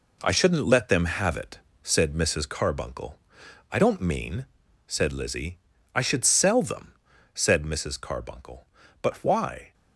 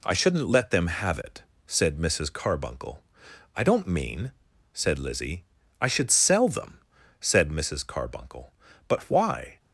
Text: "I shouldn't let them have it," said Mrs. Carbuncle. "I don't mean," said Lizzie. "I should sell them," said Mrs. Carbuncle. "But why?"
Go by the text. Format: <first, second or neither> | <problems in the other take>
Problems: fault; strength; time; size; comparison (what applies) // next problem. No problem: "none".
second | gets quieter; strong; throughout; 7.5 dB